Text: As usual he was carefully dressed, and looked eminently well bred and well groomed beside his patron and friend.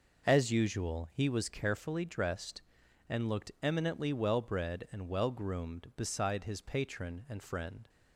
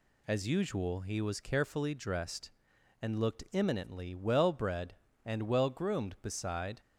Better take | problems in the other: first | stops before "his patron and friend"; at 6.7 s

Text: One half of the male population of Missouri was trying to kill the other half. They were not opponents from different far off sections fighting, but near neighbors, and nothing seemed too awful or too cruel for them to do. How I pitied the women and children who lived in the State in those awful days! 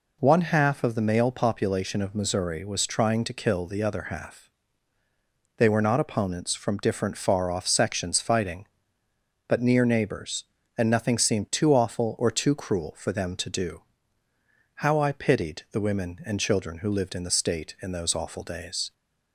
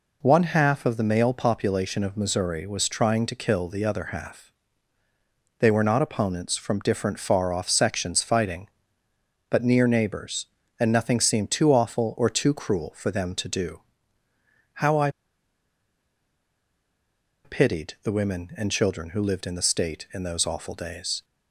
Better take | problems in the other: first | pauses between "I" and "pitied"; strong; at 15.0 s; 2.3 s long

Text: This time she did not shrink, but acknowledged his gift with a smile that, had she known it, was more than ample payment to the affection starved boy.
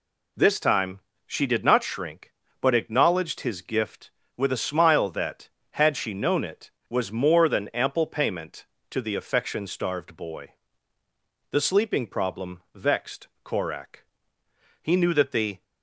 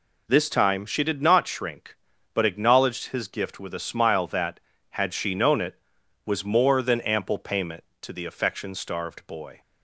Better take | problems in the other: second | pauses between "time" and "she"; slight; at 1.0 s; 0.26 s long // goes on to say "The sleeping problem vexed Korak He knew that the"; strong; from 11.5 s on; 4.1 s long

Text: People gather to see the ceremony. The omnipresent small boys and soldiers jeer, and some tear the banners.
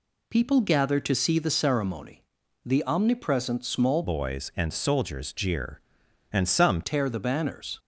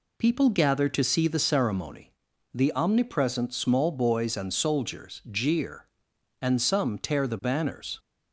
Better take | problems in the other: second | changes voice from "boys" to "some"; from 4.0 to 6.8 s; 2.8 s long

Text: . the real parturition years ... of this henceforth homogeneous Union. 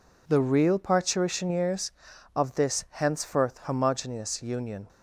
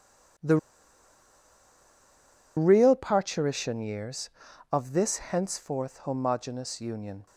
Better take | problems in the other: first | pauses between "the" and "real"; strong; at 0.5 s; 2.0 s long

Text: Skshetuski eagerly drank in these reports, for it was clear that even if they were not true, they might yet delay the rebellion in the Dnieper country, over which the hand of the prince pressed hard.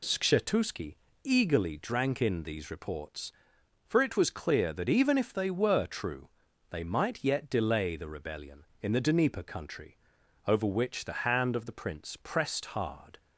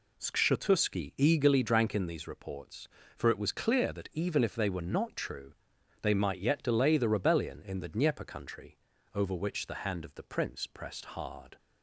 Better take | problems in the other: second | pauses between "Skshetuski" and "eagerly"; slight; at 0.9 s; 0.28 s long // skips "not"; at 5.8 s

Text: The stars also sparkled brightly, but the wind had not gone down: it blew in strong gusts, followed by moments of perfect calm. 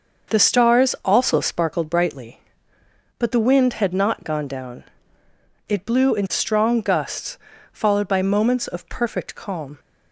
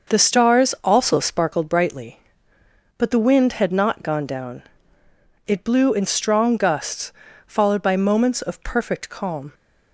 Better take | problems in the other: neither | starts louder than the rest; the same in both

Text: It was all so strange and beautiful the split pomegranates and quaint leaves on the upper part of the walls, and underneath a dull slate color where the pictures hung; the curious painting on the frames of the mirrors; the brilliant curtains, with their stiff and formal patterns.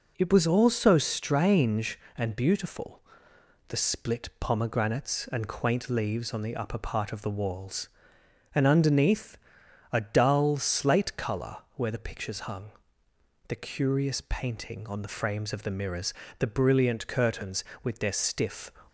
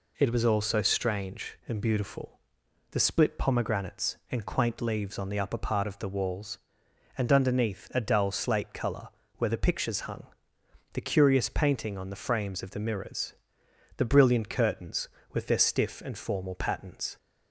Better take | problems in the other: second | pauses between "beautiful" and "the"; noticeable; at 3.0 s; 0.68 s long; noticeable in the second // pauses between "underneath" and "a"; noticeable; at 9.3 s; 0.52 s long // pauses between "color" and "where"; slight; at 11.5 s; 0.18 s long; slight in the second // stops before "and formal patterns"; at 18.8 s

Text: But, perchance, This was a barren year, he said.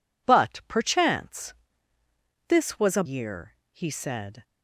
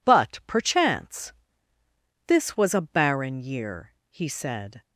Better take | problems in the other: second | skips "barren"; at 3.0 s

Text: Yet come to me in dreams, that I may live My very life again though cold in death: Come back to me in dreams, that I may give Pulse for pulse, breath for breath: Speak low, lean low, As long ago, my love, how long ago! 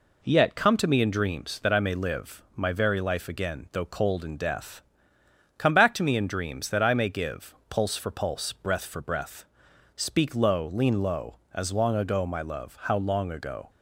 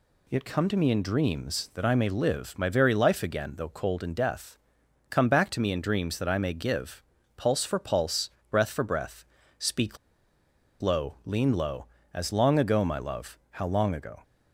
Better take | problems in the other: first | pauses between "give" and "Pulse"; slight; at 7.0 s; 0.34 s long // pauses between "Speak" and "low"; noticeable; at 9.9 s; 0.83 s long

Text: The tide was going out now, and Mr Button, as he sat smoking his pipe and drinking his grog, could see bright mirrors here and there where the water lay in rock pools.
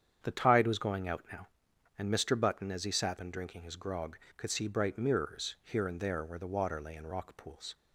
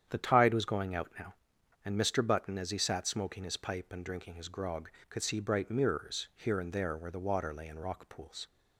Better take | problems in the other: second | starts louder than the rest; strong; until 1.2 s; 8 dB; strong in the second // skips "smoking his pipe"; at 3.1 s

